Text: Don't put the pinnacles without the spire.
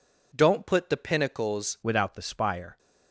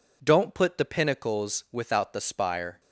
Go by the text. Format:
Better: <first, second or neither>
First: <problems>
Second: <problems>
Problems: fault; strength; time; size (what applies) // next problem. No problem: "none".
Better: second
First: changes voice at "without"; from 1.8 s on; 0.9 s long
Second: none